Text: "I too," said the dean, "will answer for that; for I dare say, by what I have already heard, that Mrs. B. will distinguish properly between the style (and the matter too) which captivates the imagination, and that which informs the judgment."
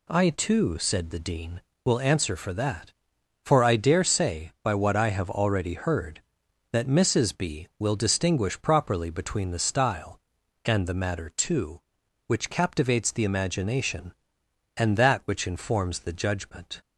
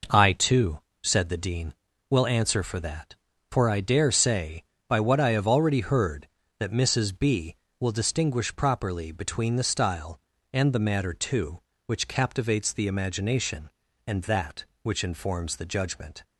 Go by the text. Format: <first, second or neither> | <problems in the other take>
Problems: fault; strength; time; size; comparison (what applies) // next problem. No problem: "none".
neither | none